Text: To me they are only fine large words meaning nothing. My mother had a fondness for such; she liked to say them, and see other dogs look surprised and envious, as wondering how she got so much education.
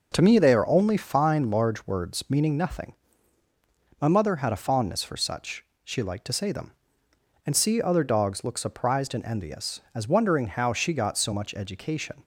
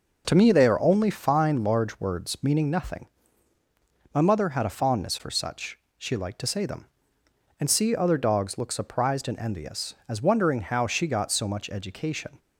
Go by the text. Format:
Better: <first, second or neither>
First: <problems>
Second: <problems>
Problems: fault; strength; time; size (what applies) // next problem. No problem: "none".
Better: neither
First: none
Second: none